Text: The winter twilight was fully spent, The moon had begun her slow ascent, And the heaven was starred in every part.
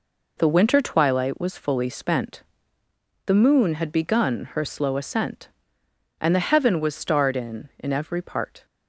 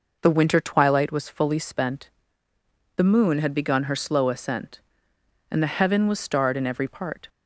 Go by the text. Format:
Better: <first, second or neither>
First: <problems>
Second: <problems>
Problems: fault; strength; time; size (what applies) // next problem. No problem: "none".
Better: second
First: says "in" twice; at 7.7 s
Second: none